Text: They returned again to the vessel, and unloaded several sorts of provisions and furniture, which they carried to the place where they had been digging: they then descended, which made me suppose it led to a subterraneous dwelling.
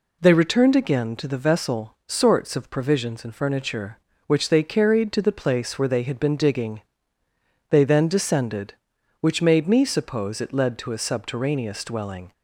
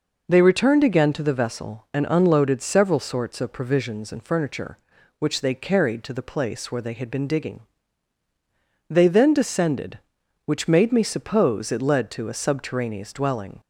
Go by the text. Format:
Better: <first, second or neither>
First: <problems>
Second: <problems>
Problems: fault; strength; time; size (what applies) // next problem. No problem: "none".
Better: second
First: skips "and unloaded several"; at 2.0 s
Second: none